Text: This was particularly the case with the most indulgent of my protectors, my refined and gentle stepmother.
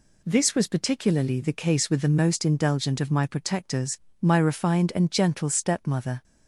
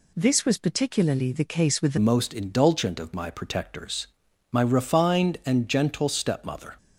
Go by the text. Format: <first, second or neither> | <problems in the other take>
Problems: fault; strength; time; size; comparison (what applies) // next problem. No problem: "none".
first | changes voice at "most"; from 1.9 s on; 4.8 s long